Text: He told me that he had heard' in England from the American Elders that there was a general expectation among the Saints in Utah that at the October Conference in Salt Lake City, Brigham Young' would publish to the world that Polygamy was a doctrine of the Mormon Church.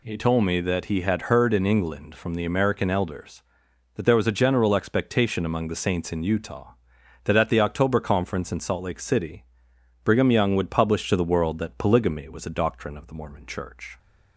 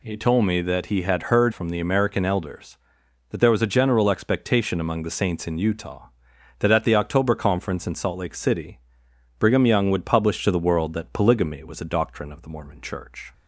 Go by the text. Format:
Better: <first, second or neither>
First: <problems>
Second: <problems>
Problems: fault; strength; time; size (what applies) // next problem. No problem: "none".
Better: first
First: none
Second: skips "in England"; at 1.5 s